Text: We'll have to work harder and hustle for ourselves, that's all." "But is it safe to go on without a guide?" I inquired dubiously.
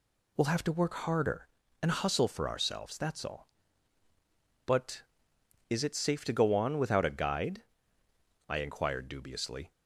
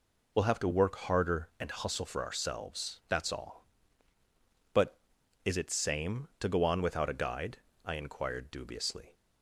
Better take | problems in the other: first | says "same" for "safe"; at 5.6 s

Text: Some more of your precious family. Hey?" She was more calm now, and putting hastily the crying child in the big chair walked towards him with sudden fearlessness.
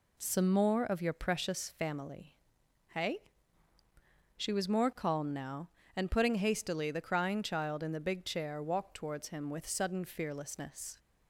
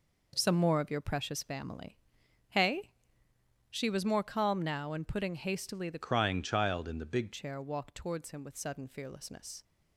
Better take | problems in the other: first | changes voice from "crying" to "big"; from 6.0 to 7.3 s; 1.3 s long

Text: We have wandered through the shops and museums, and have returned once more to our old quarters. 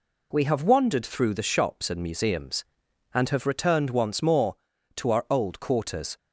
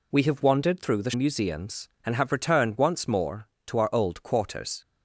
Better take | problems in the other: first | skips "shops and"; at 1.1 s

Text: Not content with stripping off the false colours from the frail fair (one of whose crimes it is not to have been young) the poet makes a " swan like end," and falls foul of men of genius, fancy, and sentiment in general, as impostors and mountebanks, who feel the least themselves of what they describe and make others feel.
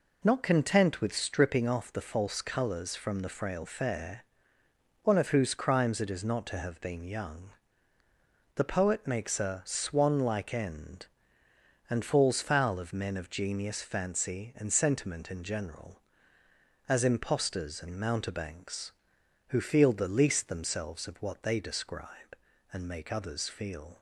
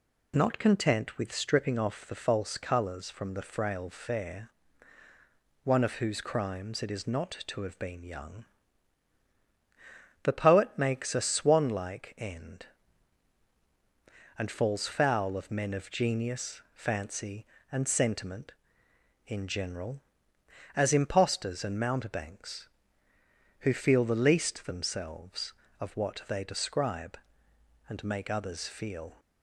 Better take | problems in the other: neither | none

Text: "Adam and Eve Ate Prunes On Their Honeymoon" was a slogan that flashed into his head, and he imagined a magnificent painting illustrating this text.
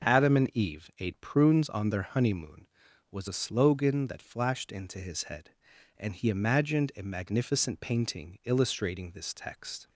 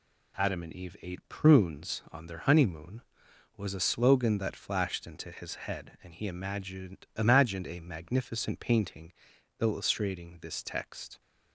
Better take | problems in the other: first | says "imagined" twice; at 7.1 s // pauses between "painting" and "illustrating"; noticeable; at 9.1 s; 0.48 s long

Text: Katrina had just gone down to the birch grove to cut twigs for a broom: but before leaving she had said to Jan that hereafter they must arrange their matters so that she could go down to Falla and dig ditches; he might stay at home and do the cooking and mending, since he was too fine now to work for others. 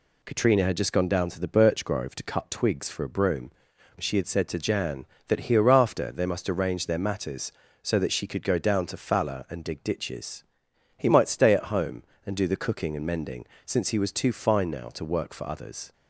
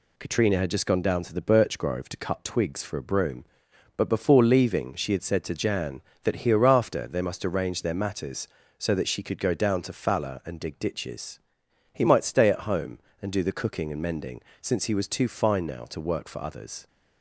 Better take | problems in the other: second | skips "but before leaving"; at 3.7 s

